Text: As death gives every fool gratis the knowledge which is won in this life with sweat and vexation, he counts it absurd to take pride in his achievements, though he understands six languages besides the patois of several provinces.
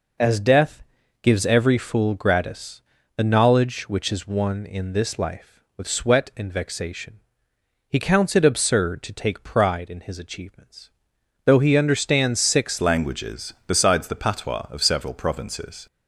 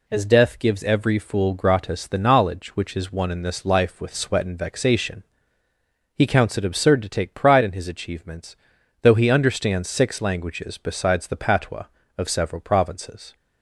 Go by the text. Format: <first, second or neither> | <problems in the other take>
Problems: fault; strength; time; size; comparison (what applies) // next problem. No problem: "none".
second | pauses between "death" and "gives"; at 0.8 s; 0.40 s long // pauses between "gratis" and "the"; slight; at 2.8 s; 0.34 s long // changes voice at "languages"; from 12.8 s on; 3.0 s long